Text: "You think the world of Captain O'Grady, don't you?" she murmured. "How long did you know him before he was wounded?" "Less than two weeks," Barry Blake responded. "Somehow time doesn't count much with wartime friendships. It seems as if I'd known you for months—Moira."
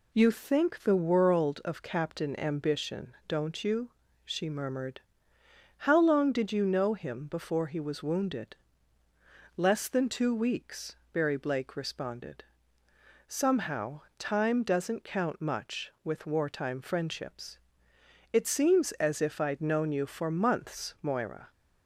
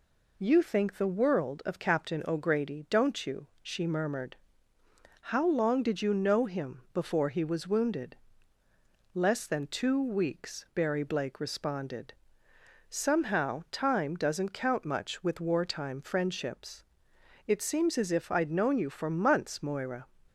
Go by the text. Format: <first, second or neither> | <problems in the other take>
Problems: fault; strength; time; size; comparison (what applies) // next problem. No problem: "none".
second | says "Ambition" for "O'Grady"; at 2.4 s // pauses between "Somehow" and "time"; slight; at 14.0 s; 0.18 s long